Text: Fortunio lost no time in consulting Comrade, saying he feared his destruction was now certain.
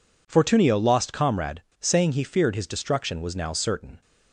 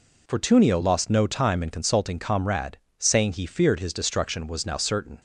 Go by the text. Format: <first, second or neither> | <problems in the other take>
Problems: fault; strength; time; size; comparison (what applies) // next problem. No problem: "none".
second | skips "no time in consulting"; at 1.1 s